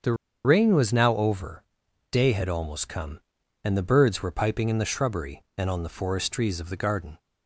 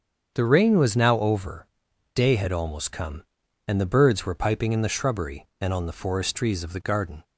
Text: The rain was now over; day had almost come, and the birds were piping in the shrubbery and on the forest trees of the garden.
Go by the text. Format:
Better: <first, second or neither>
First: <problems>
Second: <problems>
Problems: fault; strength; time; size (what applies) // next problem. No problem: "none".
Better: second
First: starts louder than the rest; strong; until 1.3 s; 7 dB // pauses between "The" and "rain"; slight; at 0.1 s; 0.31 s long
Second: starts louder than the rest; strong; until 1.3 s; 7 dB